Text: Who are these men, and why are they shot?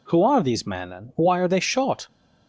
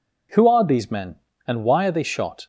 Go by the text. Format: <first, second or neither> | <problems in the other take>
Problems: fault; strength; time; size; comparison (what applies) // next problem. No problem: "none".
neither | none